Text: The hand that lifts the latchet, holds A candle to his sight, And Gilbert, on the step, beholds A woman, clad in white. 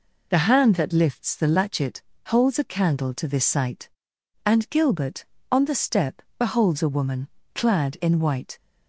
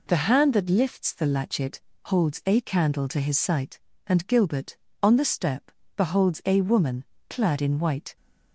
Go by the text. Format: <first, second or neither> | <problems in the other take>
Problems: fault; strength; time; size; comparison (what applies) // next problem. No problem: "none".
second | says "this" for "his"; at 3.2 s